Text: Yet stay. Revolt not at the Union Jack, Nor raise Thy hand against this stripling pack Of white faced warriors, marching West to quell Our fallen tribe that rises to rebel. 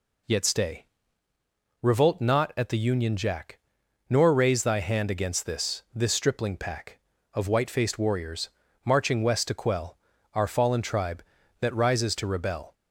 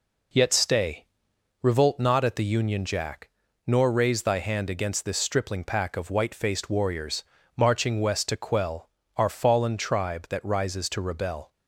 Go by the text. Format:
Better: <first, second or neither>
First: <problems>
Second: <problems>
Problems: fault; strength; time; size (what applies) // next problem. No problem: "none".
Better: second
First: says "this" twice; at 5.9 s // pauses between "quell" and "Our"; slight; at 9.9 s; 0.34 s long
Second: pauses between "quell" and "Our"; slight; at 8.8 s; 0.30 s long